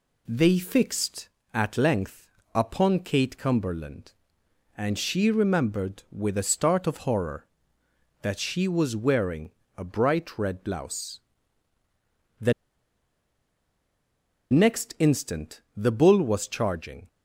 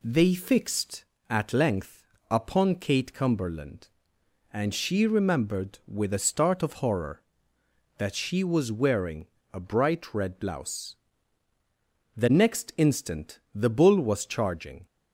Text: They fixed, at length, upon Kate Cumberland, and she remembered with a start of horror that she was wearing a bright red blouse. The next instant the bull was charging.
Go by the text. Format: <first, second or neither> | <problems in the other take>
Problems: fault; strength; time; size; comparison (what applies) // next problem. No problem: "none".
second | pauses between "wearing" and "a"; slight; at 9.5 s; 0.26 s long; slight in the second // pauses between "The" and "next"; strong; at 12.5 s; 2.0 s long